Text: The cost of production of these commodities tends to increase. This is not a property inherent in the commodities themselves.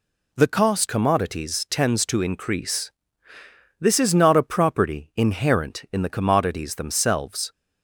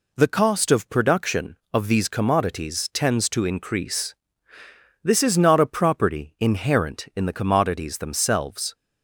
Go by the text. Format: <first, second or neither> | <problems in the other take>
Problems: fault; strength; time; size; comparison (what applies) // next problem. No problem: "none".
second | skips "of production of these"; at 0.8 s